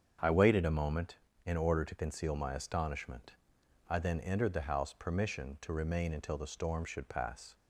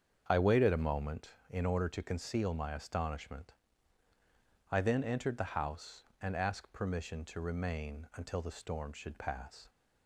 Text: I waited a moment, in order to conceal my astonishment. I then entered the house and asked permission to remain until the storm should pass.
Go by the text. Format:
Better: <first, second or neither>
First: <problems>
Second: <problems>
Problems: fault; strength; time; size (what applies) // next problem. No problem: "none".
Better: second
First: starts louder than the rest; strong; until 1.5 s; 7.5 dB // skips "and asked"; at 4.9 s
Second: starts louder than the rest; strong; until 1.2 s; 7 dB